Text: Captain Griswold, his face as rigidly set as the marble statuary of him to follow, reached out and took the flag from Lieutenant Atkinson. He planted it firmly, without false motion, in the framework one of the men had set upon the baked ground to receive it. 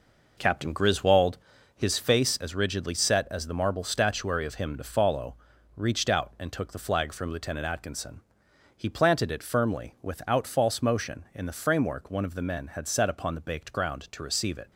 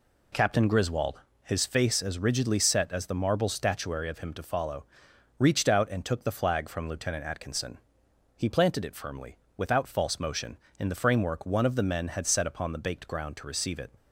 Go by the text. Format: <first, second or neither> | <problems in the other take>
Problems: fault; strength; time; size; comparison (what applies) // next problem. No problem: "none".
second | starts louder than the rest; noticeable; until 1.5 s; 5 dB